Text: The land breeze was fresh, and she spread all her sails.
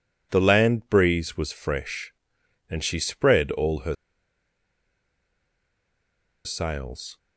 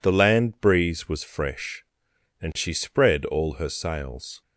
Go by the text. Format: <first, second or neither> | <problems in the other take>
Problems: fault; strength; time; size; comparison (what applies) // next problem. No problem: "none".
second | pauses between "her" and "sails"; strong; at 3.9 s; 2.5 s long